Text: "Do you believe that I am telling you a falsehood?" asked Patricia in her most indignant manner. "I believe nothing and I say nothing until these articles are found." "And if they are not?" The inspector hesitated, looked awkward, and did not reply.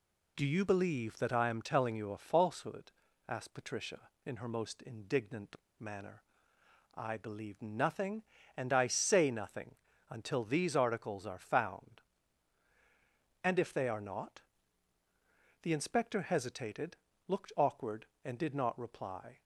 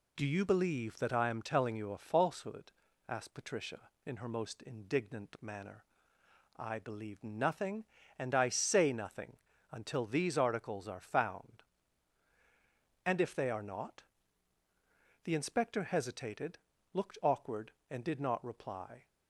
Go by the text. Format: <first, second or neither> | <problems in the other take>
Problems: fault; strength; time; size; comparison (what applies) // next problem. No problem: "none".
second | pauses between "indignant" and "manner"; slight; at 5.5 s; 0.20 s long // pauses between "nothing" and "until"; slight; at 9.7 s; 0.34 s long; slight in the second